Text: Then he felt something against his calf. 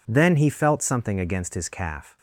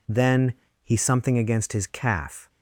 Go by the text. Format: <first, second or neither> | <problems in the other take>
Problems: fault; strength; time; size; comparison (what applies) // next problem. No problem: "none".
first | pauses between "Then" and "he"; slight; at 0.5 s; 0.30 s long // skips "felt"; at 0.9 s